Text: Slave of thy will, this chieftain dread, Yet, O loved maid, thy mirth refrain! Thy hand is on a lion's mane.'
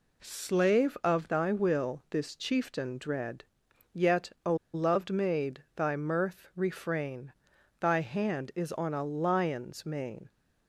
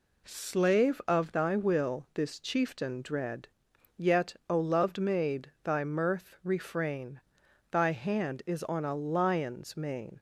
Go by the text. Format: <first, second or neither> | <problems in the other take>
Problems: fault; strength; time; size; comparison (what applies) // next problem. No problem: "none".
second | pauses between "O" and "loved"; slight; at 4.5 s; 0.19 s long